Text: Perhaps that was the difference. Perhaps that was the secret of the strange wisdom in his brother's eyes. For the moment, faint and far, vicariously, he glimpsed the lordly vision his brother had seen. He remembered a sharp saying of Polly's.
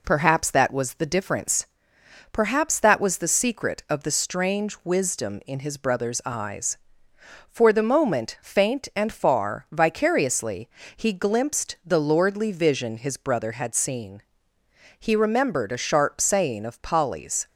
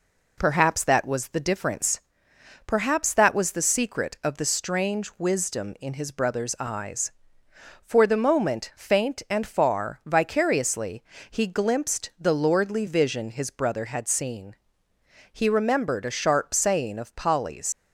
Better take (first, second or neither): first